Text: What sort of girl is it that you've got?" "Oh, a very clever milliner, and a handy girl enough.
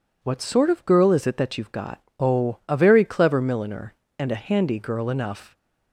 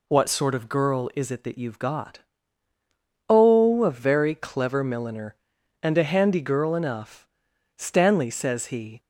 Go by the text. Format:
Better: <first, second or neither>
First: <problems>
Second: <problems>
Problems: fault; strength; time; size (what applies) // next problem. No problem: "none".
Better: first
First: none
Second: goes on to say "Stanley says he"; noticeable; from 7.7 s on; 1.2 s long